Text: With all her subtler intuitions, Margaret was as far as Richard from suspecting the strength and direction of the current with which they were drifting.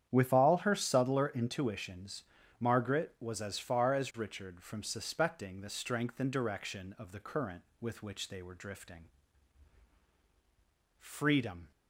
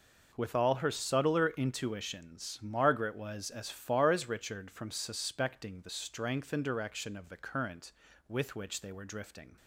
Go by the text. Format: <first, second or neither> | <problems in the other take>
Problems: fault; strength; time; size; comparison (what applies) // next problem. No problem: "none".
second | starts louder than the rest; strong; until 1.1 s; 9 dB // goes on to say "Freedom"; noticeable; from 10.9 s on; 0.72 s long